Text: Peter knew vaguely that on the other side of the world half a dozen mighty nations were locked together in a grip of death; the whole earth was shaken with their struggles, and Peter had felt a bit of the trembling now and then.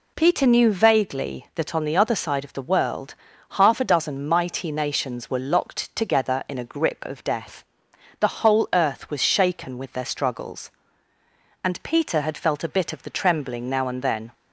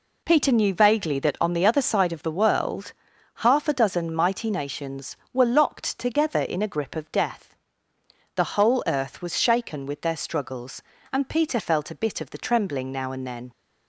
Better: first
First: pauses between "world" and "half"; at 3.1 s; 0.38 s long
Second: pauses between "world" and "half"; at 2.9 s; 0.44 s long // skips "had"; at 11.5 s

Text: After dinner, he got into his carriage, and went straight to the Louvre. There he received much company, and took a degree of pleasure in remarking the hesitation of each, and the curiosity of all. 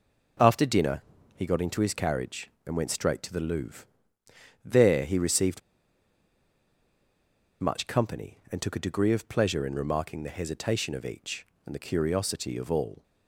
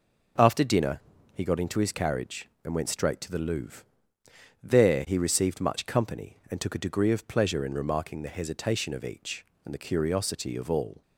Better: second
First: pauses between "received" and "much"; strong; at 5.5 s; 2.0 s long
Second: none

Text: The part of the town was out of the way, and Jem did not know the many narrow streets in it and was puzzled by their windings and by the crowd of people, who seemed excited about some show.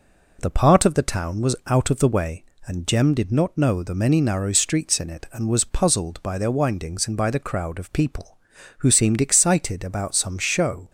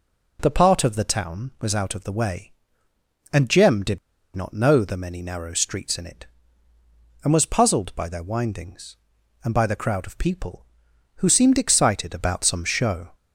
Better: first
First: none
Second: pauses between "did" and "not"; at 3.9 s; 0.37 s long

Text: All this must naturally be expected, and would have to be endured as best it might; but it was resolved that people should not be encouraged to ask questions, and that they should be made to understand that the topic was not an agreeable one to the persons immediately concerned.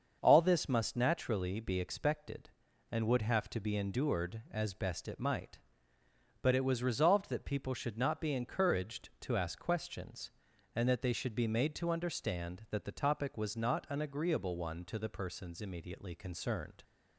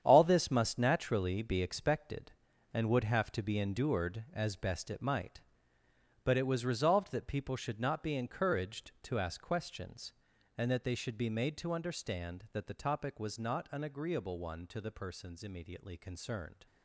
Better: first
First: starts louder than the rest; until 1.2 s; 6.5 dB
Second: gets quieter; strong; throughout; 11 dB // starts louder than the rest; strong; until 1.0 s; 9 dB

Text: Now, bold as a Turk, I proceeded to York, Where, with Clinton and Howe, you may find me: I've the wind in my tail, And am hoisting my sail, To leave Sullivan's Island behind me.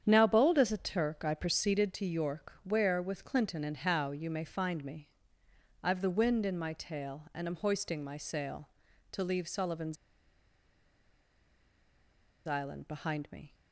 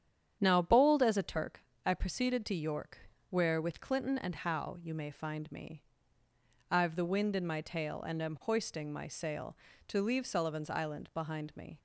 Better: second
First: starts louder than the rest; strong; until 1.0 s; 8.5 dB // pauses between "Sullivan's" and "Island"; strong; at 9.9 s; 2.5 s long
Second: starts louder than the rest; strong; until 1.4 s; 9 dB

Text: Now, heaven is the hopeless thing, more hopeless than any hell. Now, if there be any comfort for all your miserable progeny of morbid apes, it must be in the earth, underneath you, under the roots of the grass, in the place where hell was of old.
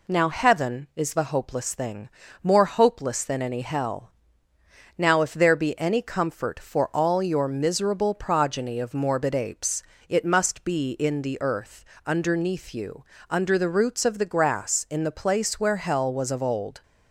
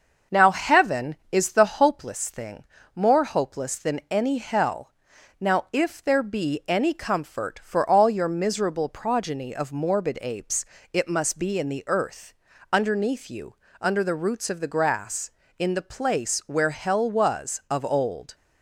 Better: first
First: none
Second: starts louder than the rest; until 2.0 s; 6 dB

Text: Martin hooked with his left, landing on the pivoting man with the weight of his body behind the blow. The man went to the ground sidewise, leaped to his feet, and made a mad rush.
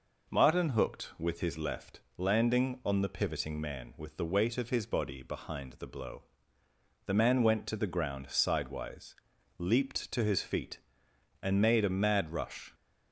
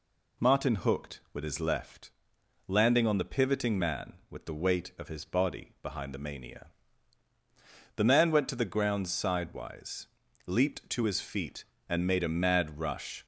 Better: first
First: none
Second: says "mania" for "blow"; at 6.1 s

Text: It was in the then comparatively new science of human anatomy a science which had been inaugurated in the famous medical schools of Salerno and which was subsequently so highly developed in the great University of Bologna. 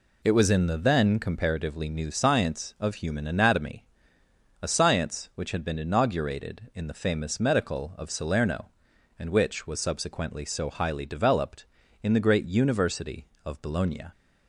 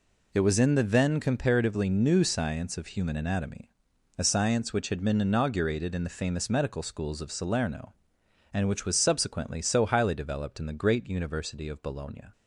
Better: second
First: pauses between "anatomy" and "a"; noticeable; at 3.8 s; 0.80 s long // skips "schools"; at 7.9 s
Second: pauses between "anatomy" and "a"; noticeable; at 3.6 s; 0.50 s long

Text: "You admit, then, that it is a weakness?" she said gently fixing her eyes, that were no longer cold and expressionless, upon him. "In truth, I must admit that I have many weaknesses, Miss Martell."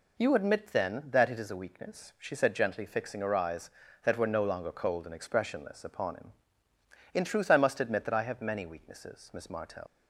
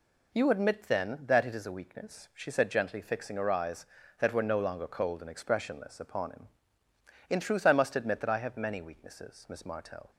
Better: second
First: leaves "Martell" unfinished; at 9.8 s; 80 ms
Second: none

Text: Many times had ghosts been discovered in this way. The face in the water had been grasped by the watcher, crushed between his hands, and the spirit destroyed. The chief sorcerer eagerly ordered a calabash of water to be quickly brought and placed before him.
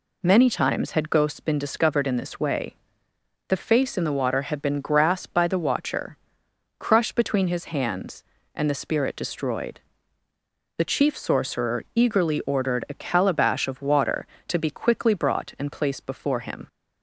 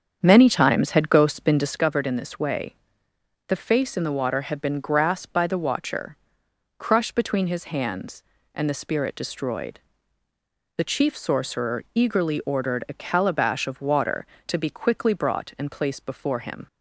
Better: first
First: none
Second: starts louder than the rest; strong; until 1.8 s; 8 dB

